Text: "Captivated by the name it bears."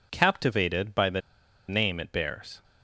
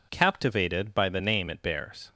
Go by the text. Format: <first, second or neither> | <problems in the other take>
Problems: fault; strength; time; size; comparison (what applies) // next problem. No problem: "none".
second | pauses between "the" and "name"; noticeable; at 1.2 s; 0.48 s long